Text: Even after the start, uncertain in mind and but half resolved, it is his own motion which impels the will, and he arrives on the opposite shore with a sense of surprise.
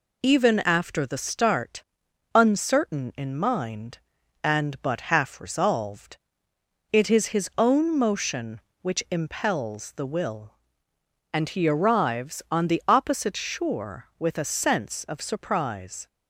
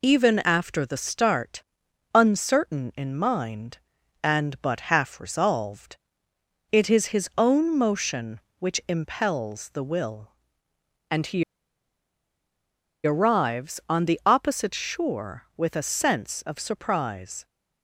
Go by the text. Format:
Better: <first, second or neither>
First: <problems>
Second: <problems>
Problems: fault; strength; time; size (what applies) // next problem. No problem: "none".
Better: first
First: none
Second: pauses between "he" and "arrives"; strong; at 11.4 s; 1.6 s long